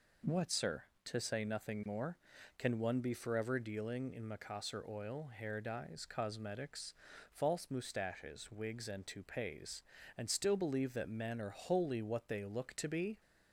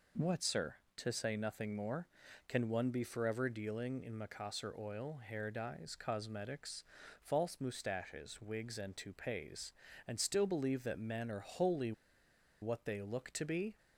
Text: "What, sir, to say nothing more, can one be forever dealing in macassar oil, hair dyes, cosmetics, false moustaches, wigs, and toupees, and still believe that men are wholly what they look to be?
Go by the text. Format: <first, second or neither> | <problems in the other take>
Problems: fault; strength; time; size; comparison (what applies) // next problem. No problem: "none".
first | pauses between "wholly" and "what"; noticeable; at 11.9 s; 0.69 s long